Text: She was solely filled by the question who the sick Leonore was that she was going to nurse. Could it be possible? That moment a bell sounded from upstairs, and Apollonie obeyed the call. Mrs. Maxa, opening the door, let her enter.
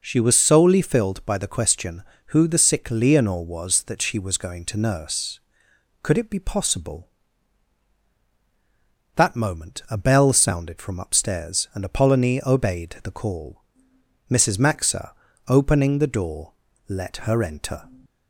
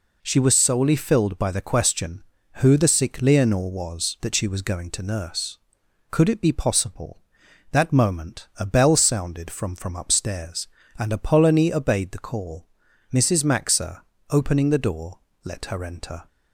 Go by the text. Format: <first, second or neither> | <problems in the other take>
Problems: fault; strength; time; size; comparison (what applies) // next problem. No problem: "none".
first | says "from" twice; at 9.7 s